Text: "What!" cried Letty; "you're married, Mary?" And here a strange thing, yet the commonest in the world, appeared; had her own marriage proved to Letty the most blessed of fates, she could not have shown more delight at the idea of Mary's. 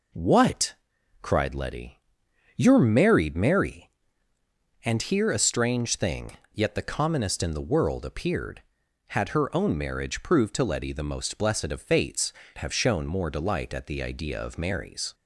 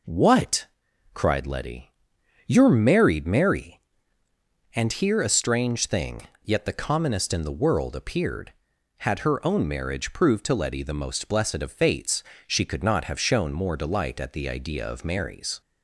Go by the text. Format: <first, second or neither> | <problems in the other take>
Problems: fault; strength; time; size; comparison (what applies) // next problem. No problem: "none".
second | skips "she could not"; at 12.4 s